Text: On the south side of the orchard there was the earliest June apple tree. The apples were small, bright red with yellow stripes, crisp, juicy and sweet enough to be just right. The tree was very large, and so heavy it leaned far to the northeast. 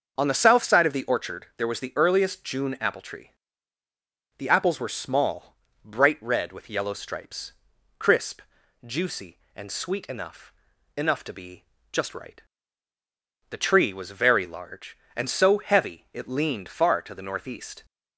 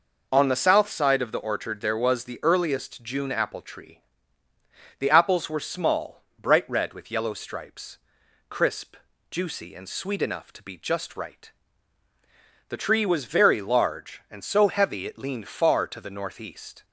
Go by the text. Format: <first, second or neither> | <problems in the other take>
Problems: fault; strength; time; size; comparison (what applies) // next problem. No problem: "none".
second | starts louder than the rest; until 1.1 s; 6.5 dB // says "enough" twice; at 10.9 s // pauses between "be" and "just"; slight; at 11.6 s; 0.28 s long